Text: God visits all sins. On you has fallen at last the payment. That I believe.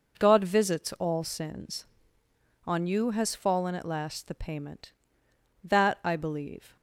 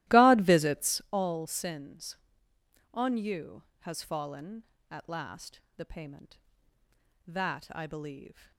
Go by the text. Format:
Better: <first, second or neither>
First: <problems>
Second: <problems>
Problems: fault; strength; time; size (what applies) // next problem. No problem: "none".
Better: first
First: none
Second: starts louder than the rest; strong; until 1.1 s; 16 dB // pauses between "last" and "the"; slight; at 5.6 s; 0.16 s long